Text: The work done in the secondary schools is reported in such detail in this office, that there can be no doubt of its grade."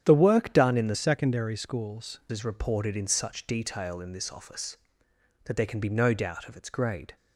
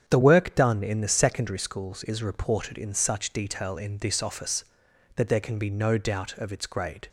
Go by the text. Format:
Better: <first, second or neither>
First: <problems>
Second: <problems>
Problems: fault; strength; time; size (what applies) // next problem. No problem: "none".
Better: second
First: starts louder than the rest; strong; until 1.0 s; 9.5 dB // changes voice from "secondary" to "schools"; from 0.9 to 2.2 s; 1.3 s long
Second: starts louder than the rest; strong; until 1.0 s; 8.5 dB